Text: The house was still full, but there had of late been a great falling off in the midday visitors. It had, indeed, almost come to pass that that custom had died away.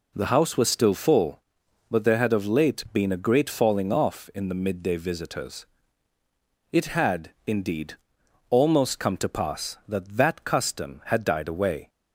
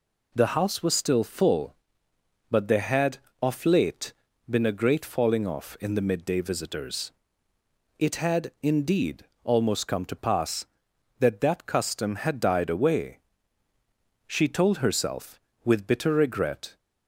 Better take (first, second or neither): first